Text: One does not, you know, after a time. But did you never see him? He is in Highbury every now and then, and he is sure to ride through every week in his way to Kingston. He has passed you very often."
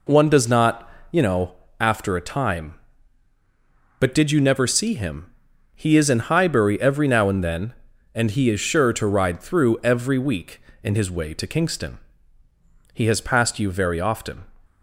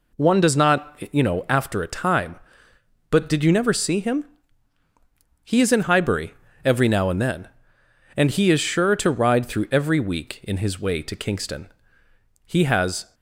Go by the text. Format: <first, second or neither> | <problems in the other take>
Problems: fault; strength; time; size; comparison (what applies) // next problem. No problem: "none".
first | pauses between "Highbury" and "every"; slight; at 6.3 s; 0.30 s long // stops before "passed you very often"; at 13.1 s